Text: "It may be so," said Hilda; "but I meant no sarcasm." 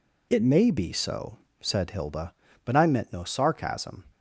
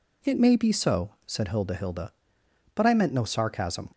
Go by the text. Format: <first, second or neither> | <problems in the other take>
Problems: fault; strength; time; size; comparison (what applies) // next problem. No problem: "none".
first | says "Hilda" twice; at 1.7 s